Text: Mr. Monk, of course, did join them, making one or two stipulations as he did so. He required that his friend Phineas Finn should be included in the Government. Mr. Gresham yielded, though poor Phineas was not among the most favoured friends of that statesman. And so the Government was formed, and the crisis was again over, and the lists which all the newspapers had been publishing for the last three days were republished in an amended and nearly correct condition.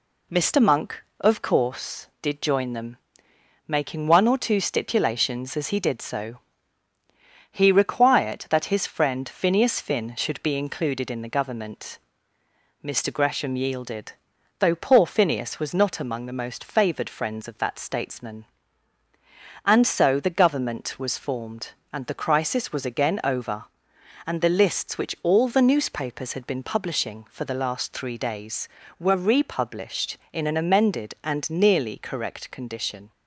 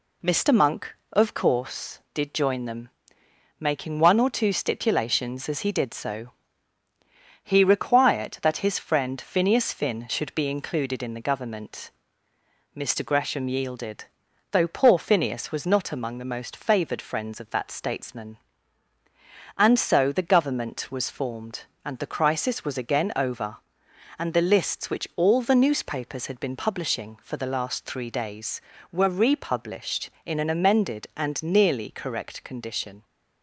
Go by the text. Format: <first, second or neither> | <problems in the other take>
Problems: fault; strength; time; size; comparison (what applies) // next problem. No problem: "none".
neither | none